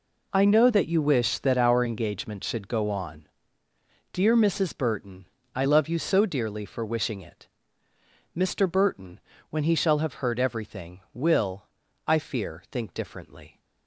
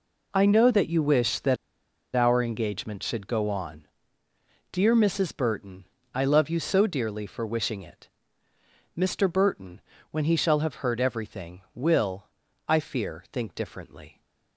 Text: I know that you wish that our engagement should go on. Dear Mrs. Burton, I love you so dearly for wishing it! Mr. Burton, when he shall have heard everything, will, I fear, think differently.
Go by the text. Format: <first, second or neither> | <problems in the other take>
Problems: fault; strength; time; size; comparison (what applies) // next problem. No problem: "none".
first | pauses between "that" and "our"; noticeable; at 1.5 s; 0.59 s long